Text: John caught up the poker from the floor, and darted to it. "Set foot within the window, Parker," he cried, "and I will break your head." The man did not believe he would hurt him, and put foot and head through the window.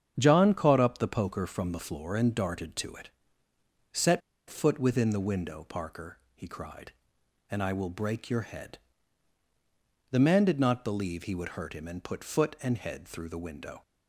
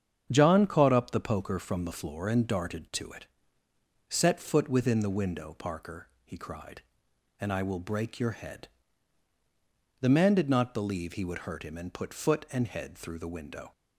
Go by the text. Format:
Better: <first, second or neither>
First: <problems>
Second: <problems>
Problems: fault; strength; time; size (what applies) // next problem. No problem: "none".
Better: second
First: starts louder than the rest; strong; until 1.1 s; 7.5 dB // pauses between "Set" and "foot"; slight; at 4.2 s; 0.29 s long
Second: starts louder than the rest; strong; until 1.3 s; 7.5 dB